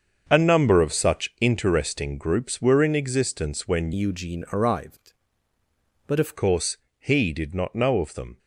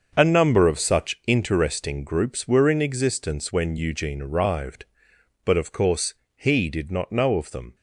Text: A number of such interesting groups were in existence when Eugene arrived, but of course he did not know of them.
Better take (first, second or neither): second